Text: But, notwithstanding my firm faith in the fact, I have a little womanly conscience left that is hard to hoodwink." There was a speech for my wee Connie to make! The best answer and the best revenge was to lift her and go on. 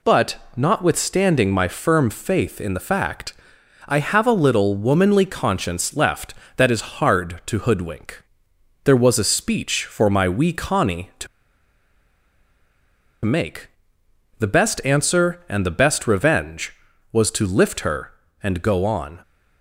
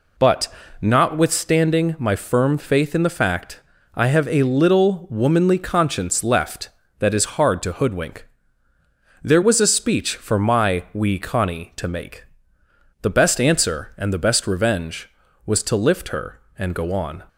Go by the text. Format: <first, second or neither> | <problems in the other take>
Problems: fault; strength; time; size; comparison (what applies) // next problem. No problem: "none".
second | pauses between "to" and "make"; strong; at 11.2 s; 1.9 s long